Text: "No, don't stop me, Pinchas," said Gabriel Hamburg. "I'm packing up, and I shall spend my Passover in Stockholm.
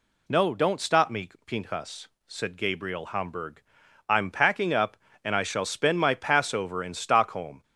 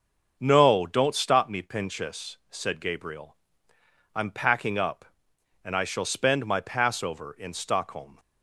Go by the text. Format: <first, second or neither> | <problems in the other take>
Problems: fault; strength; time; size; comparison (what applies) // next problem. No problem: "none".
first | starts louder than the rest; until 1.4 s; 6.5 dB // skips "Hamburg"; at 3.7 s